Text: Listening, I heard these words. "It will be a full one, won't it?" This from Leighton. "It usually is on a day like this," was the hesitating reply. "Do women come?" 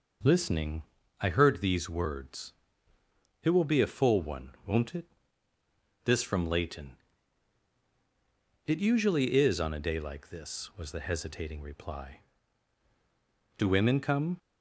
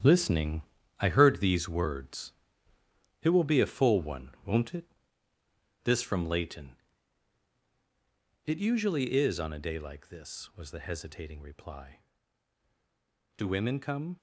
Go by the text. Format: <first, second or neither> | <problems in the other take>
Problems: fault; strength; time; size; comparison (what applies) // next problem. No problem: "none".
first | gets quieter; strong; throughout; 10 dB